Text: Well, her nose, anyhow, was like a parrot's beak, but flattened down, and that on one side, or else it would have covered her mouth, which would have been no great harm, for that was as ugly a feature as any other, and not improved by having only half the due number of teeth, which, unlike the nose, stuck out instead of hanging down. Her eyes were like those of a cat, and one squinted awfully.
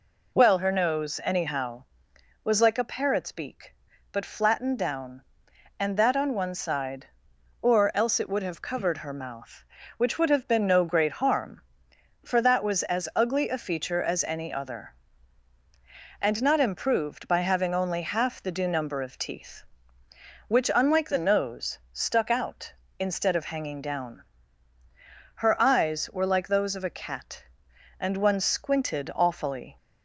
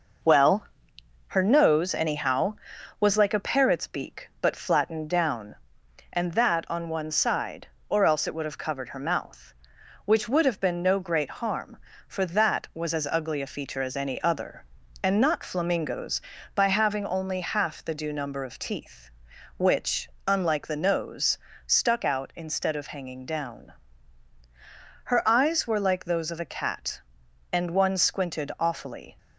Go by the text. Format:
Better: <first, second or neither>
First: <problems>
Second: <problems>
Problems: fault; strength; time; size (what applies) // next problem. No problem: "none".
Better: first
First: none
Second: says "flamingos" for "improved"; at 15.4 s